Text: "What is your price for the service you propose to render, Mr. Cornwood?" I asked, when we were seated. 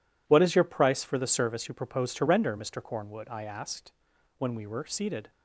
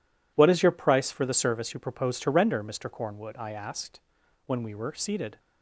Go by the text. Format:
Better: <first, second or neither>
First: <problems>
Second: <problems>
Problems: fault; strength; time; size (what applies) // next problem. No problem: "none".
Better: neither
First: none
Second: none